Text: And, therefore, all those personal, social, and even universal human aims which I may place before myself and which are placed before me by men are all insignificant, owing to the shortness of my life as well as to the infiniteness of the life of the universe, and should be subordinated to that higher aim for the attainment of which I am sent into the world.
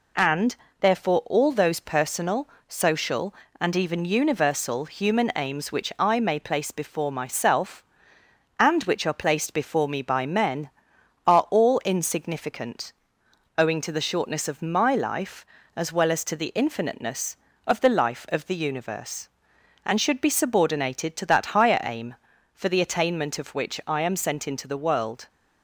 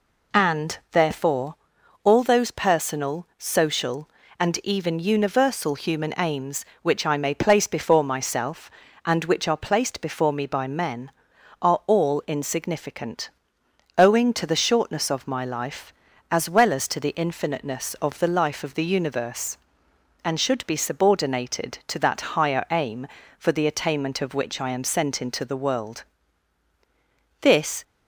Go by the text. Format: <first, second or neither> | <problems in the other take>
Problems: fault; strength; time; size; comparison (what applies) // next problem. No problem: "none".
first | goes on to say "This"; slight; from 27.4 s on; 0.42 s long